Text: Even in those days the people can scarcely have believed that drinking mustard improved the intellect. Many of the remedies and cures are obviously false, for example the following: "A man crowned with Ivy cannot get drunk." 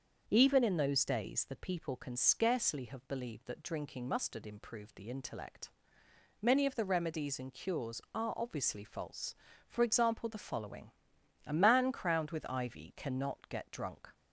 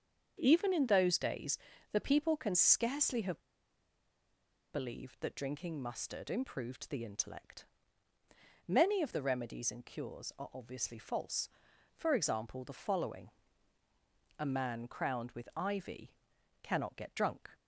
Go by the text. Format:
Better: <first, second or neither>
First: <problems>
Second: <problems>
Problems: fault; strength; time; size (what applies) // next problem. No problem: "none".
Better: first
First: starts louder than the rest; until 1.2 s; 6.5 dB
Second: starts louder than the rest; until 1.3 s; 7 dB // pauses between "days" and "the"; slight; at 1.5 s; 0.32 s long // pauses between "have" and "believed"; strong; at 3.4 s; 1.3 s long // pauses between "Ivy" and "cannot"; noticeable; at 16.1 s; 0.50 s long